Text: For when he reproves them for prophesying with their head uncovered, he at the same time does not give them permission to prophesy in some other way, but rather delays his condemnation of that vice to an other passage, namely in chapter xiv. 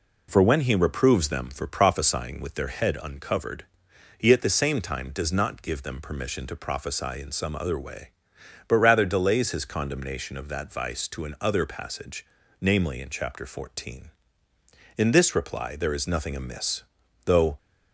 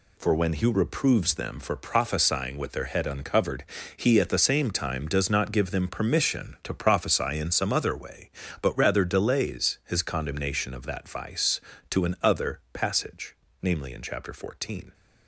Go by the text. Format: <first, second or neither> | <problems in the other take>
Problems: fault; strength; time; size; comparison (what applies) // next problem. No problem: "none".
second | goes on to say "In this reply there is nothing amiss though"; strong; from 14.9 s on; 2.6 s long